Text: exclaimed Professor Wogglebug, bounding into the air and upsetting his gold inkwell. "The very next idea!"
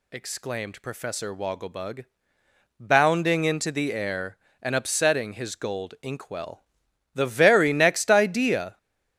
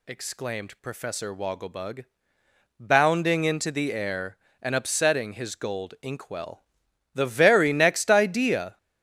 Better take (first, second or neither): neither